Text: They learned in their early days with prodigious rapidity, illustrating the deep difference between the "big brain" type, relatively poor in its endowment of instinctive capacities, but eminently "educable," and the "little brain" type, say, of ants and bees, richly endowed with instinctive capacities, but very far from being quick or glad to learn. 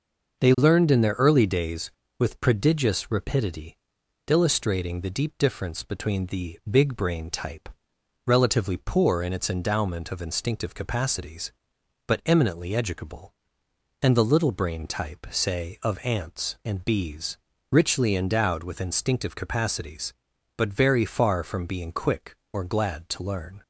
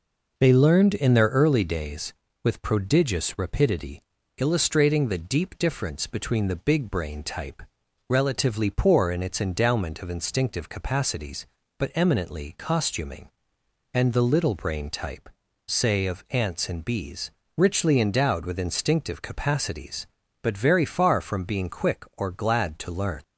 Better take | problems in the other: first | says "costuming" for "educable"; at 12.5 s

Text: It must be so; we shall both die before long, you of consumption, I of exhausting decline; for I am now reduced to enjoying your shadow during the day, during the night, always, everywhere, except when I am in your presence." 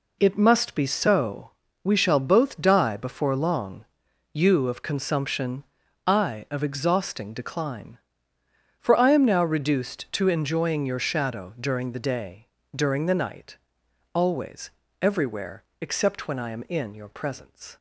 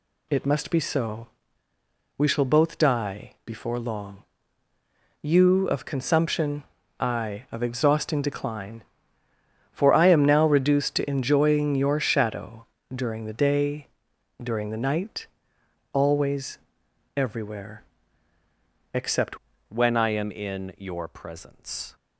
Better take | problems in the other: first | pauses between "shadow" and "during"; slight; at 12.6 s; 0.28 s long // changes voice at "when"; from 19.6 s on; 2.3 s long

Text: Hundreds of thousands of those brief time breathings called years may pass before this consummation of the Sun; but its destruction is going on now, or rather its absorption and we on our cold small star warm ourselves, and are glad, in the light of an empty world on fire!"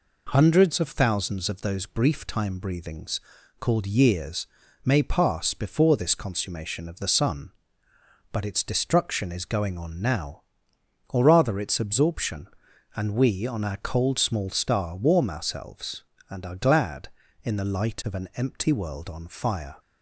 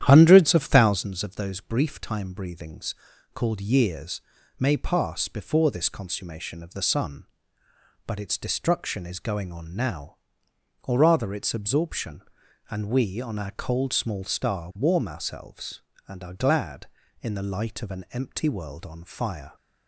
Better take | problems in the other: first | starts louder than the rest; strong; until 1.1 s; 10.5 dB // pauses between "breathings" and "called"; at 2.9 s; 0.40 s long; also in the first // pauses between "years" and "may"; at 4.1 s; 0.38 s long; also in the first

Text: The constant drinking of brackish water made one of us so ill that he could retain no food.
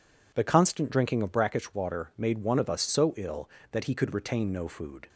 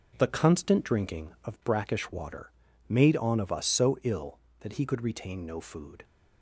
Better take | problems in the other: first | pauses between "water" and "made"; slight; at 2.5 s; 0.36 s long // says "on" for "one"; at 3.1 s

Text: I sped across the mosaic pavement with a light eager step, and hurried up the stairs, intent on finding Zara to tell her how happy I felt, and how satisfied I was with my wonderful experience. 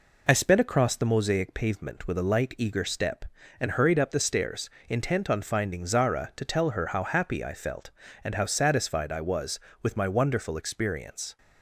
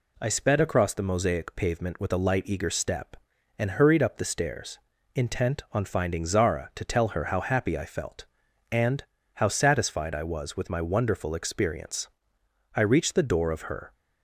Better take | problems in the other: first | pauses between "and" and "how"; slight; at 9.0 s; 0.32 s long // goes on to say "I reached the door of her"; noticeable; from 12.7 s on; 1.1 s long

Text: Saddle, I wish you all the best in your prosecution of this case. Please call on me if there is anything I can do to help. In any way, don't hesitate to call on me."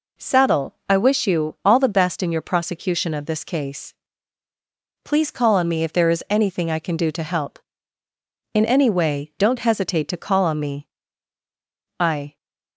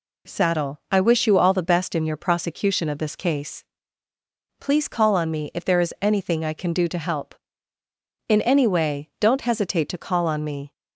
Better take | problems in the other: second | goes on to say "I"; slight; from 12.0 s on; 0.36 s long

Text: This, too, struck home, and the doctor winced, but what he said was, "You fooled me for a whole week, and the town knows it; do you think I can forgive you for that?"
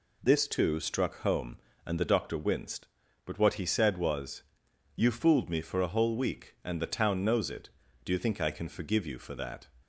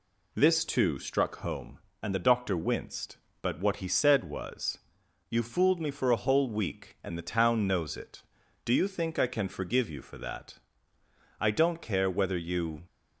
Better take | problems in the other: first | goes on to say "I don't care whether you"; from 11.4 s on; 1.4 s long

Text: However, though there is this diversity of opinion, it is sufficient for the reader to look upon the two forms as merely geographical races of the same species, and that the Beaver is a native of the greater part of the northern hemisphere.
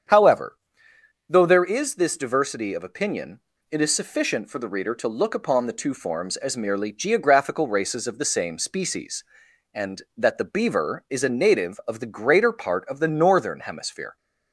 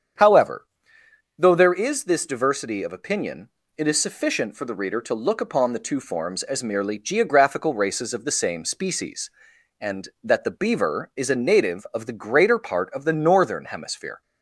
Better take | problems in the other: neither | starts louder than the rest; strong; the same in both

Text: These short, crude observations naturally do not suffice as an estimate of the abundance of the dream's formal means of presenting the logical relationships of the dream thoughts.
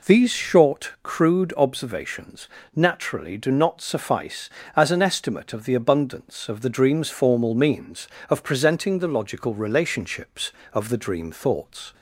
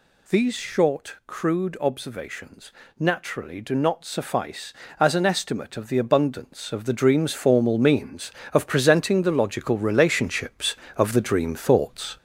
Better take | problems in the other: first | gets louder; noticeable; throughout; 4 dB // pauses between "observations" and "naturally"; slight; at 2.7 s; 0.28 s long; slight in the first

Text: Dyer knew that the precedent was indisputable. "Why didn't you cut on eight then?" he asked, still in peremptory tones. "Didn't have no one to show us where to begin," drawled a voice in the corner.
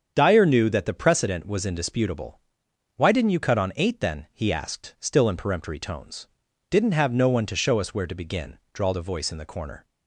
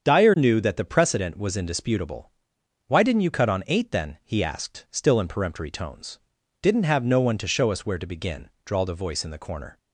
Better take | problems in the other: neither | starts louder than the rest; strong; the same in both

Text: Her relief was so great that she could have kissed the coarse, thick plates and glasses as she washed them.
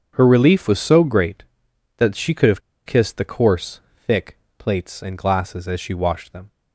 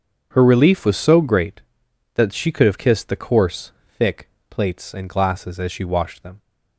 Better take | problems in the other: second | starts louder than the rest; strong; until 1.1 s; 7.5 dB; strong in the second // pauses between "have" and "kissed"; slight; at 2.5 s; 0.26 s long // pauses between "thick" and "plates"; slight; at 4.3 s; 0.22 s long; slight in the second

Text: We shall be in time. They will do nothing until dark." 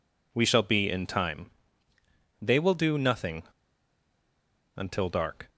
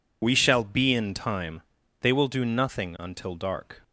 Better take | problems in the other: second | pauses between "nothing" and "until"; strong; at 3.4 s; 1.3 s long

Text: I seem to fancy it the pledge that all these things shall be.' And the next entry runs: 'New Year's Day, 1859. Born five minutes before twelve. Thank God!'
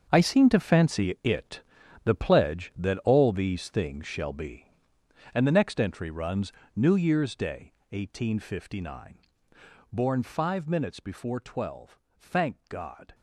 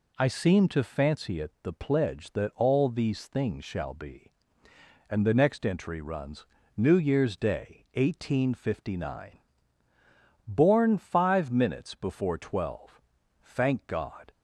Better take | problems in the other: second | gets quieter; strong; throughout; 11.5 dB // pauses between "it" and "the"; at 1.6 s; 0.44 s long

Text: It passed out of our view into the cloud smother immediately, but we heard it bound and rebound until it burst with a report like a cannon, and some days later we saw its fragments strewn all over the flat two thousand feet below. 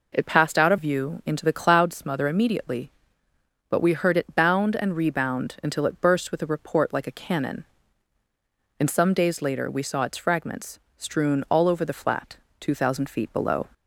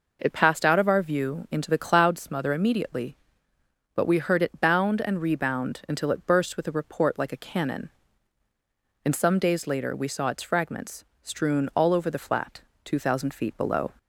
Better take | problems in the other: second | skips "our"; at 0.7 s // pauses between "fragments" and "strewn"; slight; at 10.7 s; 0.18 s long; slight in the second // pauses between "flat" and "two"; slight; at 12.3 s; 0.22 s long; slight in the second

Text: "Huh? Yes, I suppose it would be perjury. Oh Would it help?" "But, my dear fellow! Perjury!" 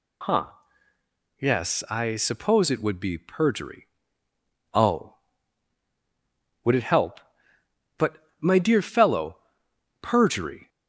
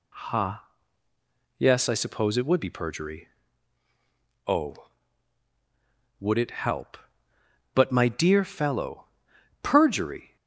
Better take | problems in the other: neither | none

